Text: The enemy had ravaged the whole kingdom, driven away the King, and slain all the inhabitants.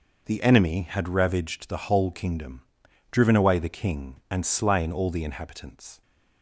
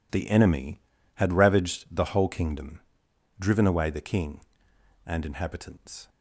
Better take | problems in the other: first | skips "slain all the"; at 5.2 s

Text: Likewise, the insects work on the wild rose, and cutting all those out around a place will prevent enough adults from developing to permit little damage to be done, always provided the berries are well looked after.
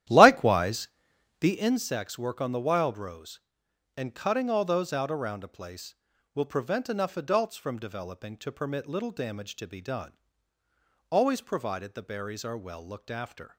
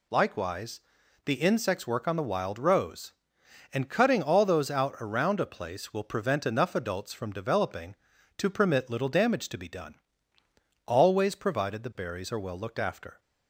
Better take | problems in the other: second | starts louder than the rest; strong; until 1.8 s; 12.5 dB

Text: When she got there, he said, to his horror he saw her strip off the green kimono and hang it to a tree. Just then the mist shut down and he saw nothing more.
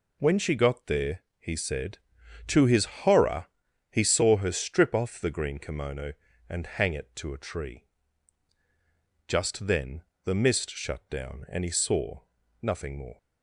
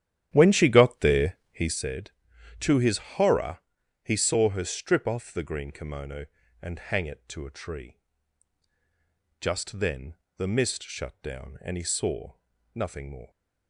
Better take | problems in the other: first | starts louder than the rest; strong; until 1.9 s; 12 dB // pauses between "his" and "horror"; slight; at 2.9 s; 0.18 s long; slight in the first // pauses between "horror" and "he"; noticeable; at 3.5 s; 0.46 s long; noticeable in the first // pauses between "then" and "the"; slight; at 10.1 s; 0.22 s long; slight in the first // pauses between "saw" and "nothing"; at 12.3 s; 0.42 s long; also in the first

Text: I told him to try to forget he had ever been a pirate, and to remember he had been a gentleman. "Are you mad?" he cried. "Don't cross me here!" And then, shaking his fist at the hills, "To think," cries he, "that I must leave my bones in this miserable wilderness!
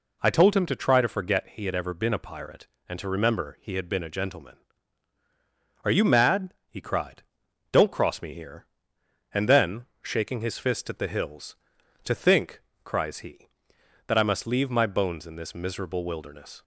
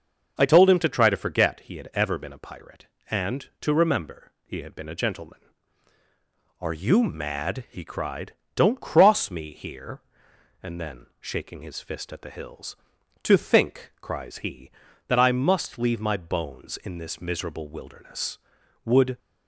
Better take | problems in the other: first | starts louder than the rest; noticeable; until 1.3 s; 6 dB // goes on to say "Would"; slight; from 18.8 s on; 0.32 s long

